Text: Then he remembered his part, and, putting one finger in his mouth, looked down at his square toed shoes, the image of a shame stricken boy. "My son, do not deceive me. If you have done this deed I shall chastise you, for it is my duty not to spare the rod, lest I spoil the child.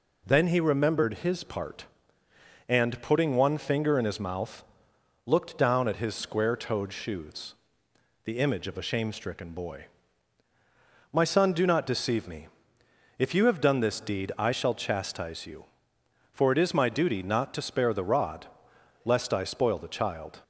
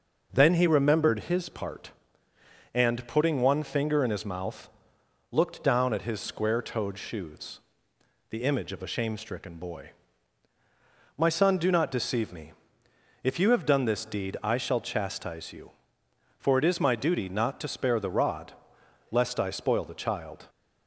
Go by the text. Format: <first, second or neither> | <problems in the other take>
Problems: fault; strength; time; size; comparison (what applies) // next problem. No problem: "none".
first | starts louder than the rest; noticeable; until 1.5 s; 5.5 dB